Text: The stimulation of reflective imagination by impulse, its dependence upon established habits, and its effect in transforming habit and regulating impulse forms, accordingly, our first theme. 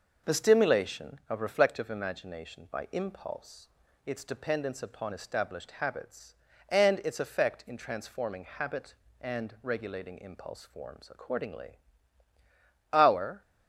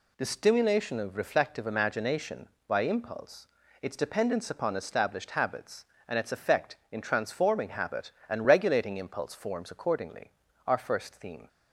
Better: second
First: stops before "first theme"; at 13.4 s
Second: none

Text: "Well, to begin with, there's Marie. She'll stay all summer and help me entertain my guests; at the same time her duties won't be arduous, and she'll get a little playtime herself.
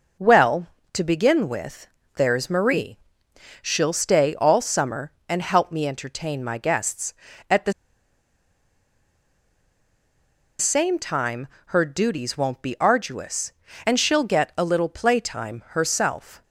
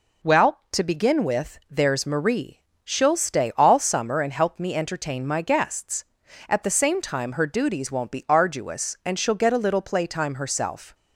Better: second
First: pauses between "the" and "same"; strong; at 7.7 s; 2.8 s long // pauses between "time" and "her"; slight; at 11.4 s; 0.20 s long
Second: none

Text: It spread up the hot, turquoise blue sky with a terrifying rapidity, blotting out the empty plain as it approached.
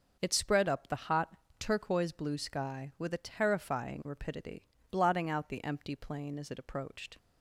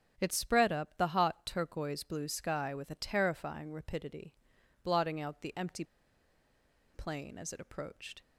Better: first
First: starts louder than the rest; noticeable; until 1.2 s; 6 dB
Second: starts louder than the rest; strong; until 1.1 s; 7 dB // pauses between "empty" and "plain"; at 5.8 s; 1.0 s long

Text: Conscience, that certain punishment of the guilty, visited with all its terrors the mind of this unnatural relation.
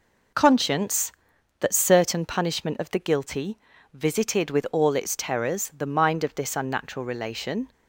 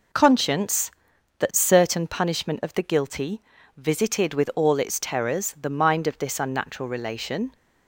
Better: neither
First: none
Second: none

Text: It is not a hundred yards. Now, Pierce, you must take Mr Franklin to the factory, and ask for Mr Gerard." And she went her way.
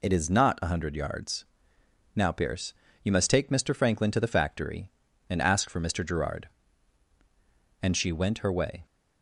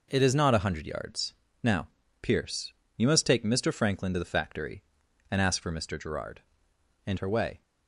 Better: first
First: none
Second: skips "she went"; at 7.1 s

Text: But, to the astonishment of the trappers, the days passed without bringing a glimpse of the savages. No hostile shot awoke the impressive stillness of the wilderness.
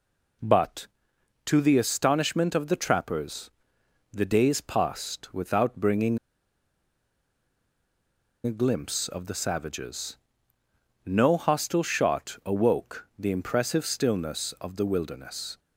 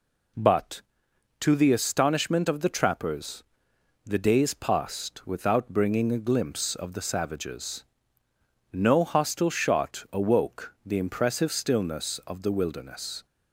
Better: second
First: pauses between "bringing" and "a"; strong; at 6.1 s; 2.2 s long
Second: none

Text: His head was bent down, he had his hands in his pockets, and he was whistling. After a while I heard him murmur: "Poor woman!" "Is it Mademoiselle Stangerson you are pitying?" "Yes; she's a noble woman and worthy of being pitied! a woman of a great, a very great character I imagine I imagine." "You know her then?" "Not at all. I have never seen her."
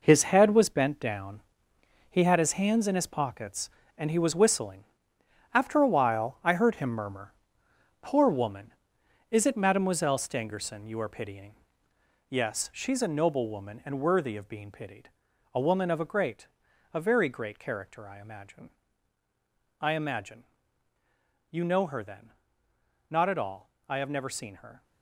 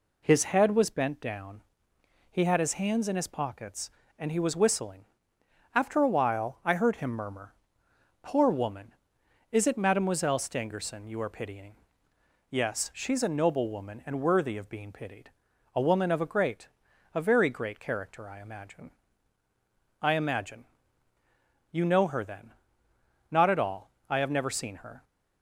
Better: second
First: gets quieter; strong; throughout; 10 dB // pauses between "imagine" and "I"; at 18.7 s; 1.0 s long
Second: pauses between "imagine" and "I"; at 18.9 s; 1.0 s long

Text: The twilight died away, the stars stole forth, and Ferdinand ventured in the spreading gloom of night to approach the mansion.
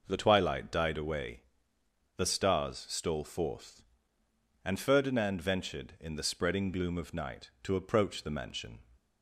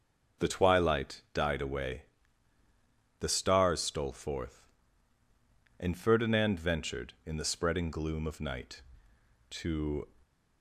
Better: first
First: none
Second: starts louder than the rest; until 1.5 s; 6 dB // stops before "approach the mansion"; at 10.2 s

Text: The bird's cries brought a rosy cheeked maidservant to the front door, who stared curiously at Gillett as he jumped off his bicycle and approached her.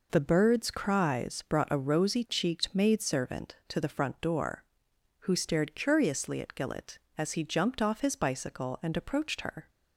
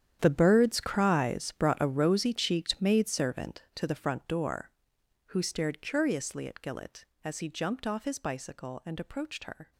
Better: first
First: none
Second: gets quieter; strong; throughout; 16.5 dB

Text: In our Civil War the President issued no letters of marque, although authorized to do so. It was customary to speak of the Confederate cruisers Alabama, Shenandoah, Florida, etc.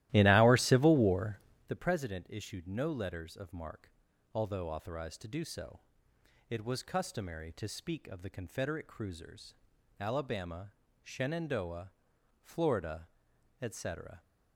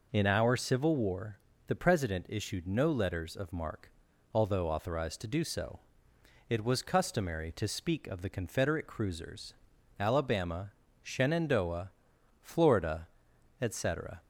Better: second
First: starts louder than the rest; strong; until 1.8 s; 15.5 dB // pauses between "War" and "the"; slight; at 1.3 s; 0.30 s long // pauses between "cruisers" and "Alabama"; noticeable; at 9.5 s; 0.46 s long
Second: pauses between "War" and "the"; slight; at 1.3 s; 0.30 s long // pauses between "cruisers" and "Alabama"; noticeable; at 9.5 s; 0.46 s long

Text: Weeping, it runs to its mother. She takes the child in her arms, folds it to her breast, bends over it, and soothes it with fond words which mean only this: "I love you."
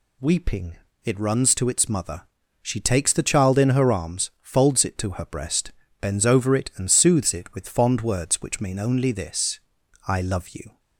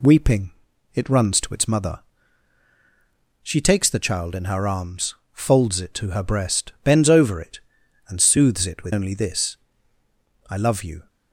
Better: first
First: none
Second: skips "fond words which mean"; at 8.9 s

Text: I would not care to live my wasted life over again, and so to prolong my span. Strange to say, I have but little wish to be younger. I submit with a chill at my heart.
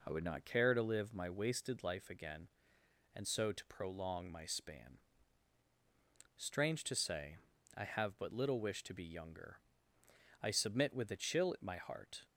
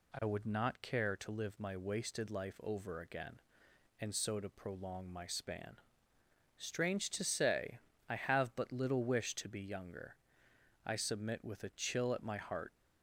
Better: second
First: skips "over"; at 2.0 s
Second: none

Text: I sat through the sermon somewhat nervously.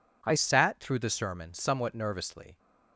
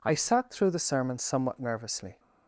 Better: second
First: changes voice at "sat"; from 0.3 s on; 2.2 s long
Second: none

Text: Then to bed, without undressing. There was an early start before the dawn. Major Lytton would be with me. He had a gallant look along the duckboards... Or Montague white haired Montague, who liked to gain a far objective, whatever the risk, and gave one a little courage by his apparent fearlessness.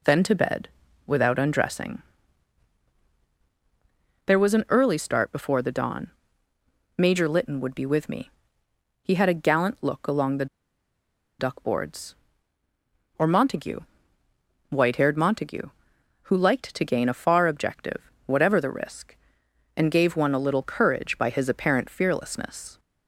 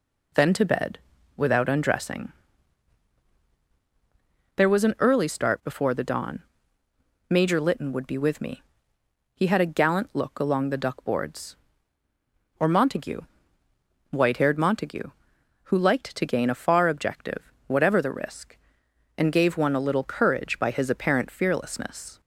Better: second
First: pauses between "the" and "duckboards"; noticeable; at 10.4 s; 0.93 s long // pauses between "Montague" and "white"; noticeable; at 13.8 s; 0.88 s long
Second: pauses between "Montague" and "white"; noticeable; at 13.2 s; 0.88 s long

